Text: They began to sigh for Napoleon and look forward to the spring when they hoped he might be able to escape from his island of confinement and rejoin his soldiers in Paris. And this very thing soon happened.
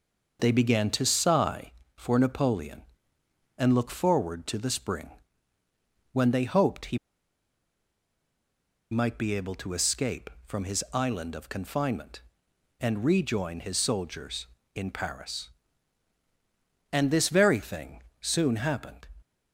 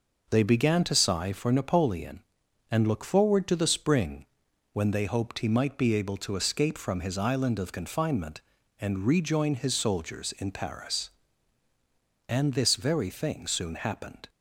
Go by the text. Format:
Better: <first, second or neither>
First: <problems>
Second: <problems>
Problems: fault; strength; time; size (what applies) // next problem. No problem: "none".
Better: second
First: pauses between "spring" and "when"; at 5.1 s; 1.0 s long // pauses between "he" and "might"; strong; at 6.9 s; 1.9 s long // pauses between "thing" and "soon"; slight; at 18.0 s; 0.18 s long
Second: pauses between "spring" and "when"; noticeable; at 4.2 s; 0.46 s long